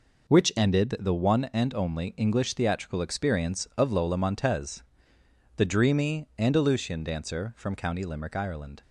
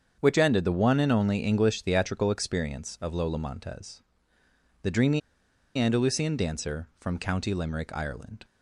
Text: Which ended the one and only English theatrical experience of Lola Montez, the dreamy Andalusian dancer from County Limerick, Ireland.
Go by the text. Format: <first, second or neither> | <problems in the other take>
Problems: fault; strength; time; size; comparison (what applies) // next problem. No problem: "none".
first | starts louder than the rest; strong; until 1.1 s; 7.5 dB // pauses between "dreamy" and "Andalusian"; noticeable; at 5.2 s; 0.58 s long